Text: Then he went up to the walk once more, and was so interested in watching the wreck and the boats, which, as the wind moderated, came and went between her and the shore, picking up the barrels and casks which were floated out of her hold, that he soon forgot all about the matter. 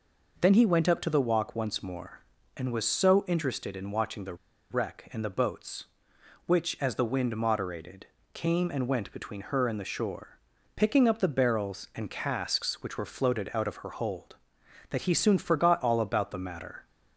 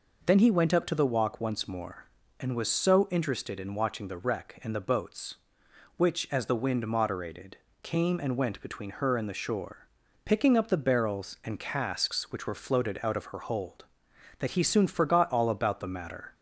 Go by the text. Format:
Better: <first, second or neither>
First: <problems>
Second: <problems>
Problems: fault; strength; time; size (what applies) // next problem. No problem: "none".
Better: second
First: pauses between "the" and "wreck"; slight; at 4.3 s; 0.35 s long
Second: none